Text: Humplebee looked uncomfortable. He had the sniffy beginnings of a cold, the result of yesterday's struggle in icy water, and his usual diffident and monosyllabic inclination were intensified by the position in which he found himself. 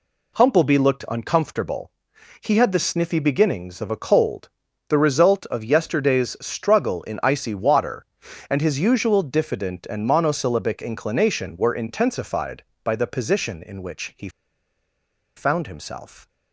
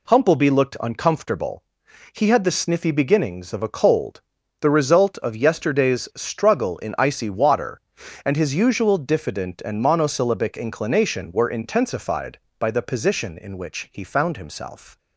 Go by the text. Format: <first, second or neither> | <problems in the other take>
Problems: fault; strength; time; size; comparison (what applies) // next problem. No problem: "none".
second | pauses between "he" and "found"; at 14.2 s; 1.0 s long